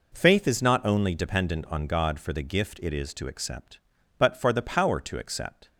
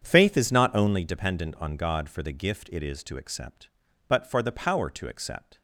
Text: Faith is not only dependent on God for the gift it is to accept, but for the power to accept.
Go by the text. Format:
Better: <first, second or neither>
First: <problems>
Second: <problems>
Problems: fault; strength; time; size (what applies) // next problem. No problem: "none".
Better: first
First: none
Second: starts louder than the rest; strong; until 1.0 s; 7.5 dB